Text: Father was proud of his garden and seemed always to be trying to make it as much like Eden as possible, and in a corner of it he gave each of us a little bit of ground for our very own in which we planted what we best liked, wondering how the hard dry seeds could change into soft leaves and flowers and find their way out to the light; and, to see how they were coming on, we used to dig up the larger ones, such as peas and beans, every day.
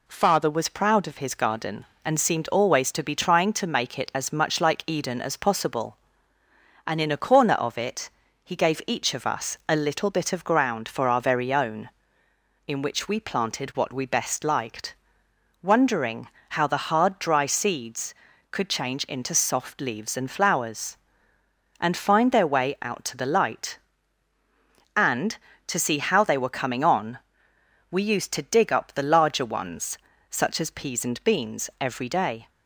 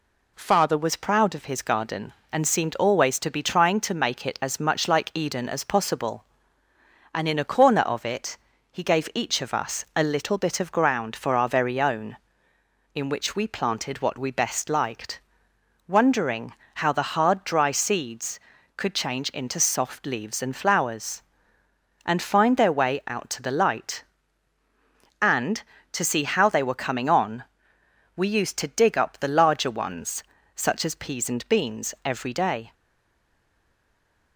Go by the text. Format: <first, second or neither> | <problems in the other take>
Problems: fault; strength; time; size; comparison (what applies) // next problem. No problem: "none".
first | pauses between "it" and "he"; slight; at 8.3 s; 0.36 s long; slight in the first // pauses between "wondering" and "how"; slight; at 16.5 s; 0.22 s long; slight in the first // stays silent after the last word; noticeable; from 32.7 s on; 1.6 s long